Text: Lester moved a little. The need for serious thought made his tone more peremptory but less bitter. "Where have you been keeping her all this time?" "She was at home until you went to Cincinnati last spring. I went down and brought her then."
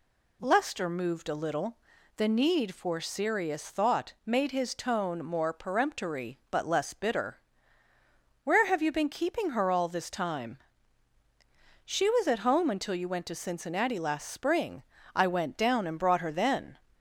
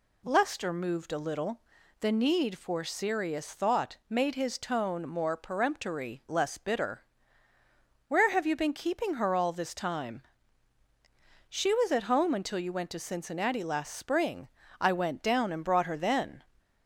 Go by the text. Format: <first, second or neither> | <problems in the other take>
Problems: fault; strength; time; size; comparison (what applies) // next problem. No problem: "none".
first | skips "but"; at 6.2 s